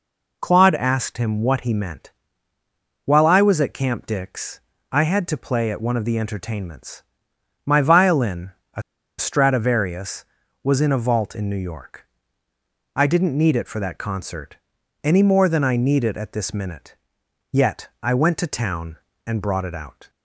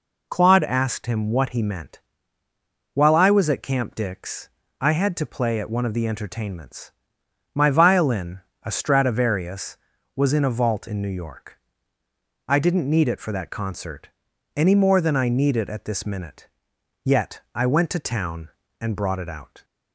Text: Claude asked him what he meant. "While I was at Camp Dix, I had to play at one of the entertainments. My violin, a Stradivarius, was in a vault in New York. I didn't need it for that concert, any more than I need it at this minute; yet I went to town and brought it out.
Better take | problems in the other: second | pauses between "a" and "Stradivarius"; at 8.8 s; 0.37 s long

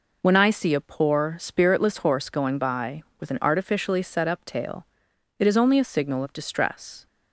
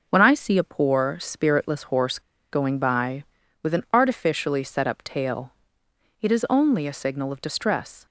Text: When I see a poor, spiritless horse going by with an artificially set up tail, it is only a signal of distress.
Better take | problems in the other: first | pauses between "horse" and "going"; slight; at 2.1 s; 0.31 s long

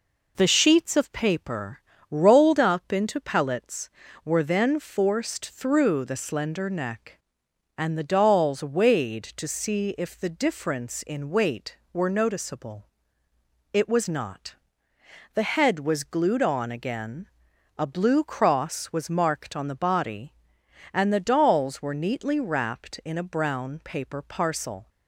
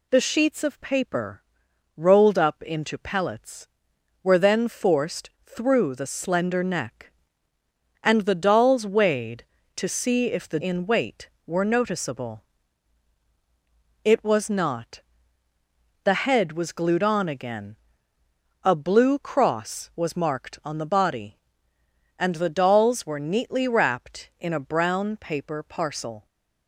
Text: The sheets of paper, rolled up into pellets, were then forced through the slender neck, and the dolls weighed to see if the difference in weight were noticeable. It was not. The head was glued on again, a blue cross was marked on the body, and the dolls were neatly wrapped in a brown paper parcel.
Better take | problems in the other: first | skips "difference"; at 10.5 s

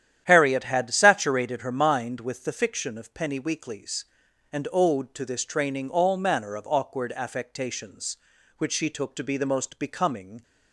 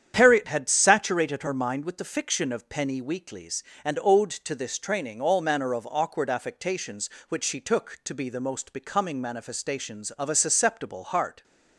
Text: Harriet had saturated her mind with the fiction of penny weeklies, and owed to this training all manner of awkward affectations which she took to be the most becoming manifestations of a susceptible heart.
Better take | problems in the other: second | starts louder than the rest; strong; until 1.2 s; 10.5 dB; strong in the second // stops before "manifestations of a susceptible heart"; at 10.4 s

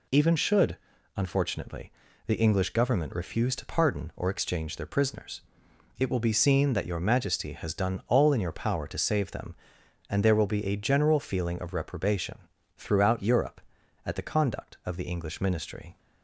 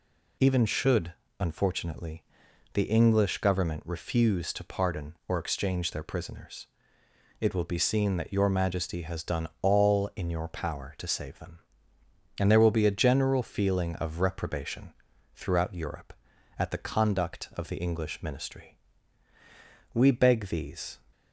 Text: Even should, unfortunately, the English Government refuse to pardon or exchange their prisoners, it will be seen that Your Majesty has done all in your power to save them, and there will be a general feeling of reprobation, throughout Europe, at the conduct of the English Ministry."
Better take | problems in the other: first | goes on to say "We beg these"; noticeable; from 19.9 s on; 1.0 s long

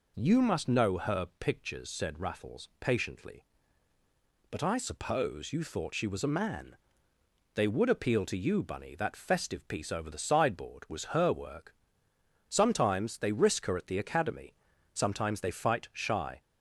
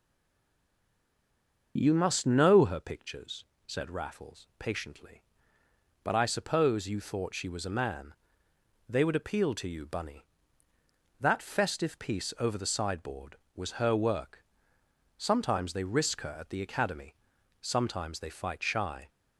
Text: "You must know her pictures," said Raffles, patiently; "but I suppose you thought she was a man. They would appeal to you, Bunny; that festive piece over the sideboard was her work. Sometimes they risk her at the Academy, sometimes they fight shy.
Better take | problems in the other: first | stays silent before the first word; noticeable; until 1.7 s; 1.7 s long // starts louder than the rest; until 2.7 s; 6 dB

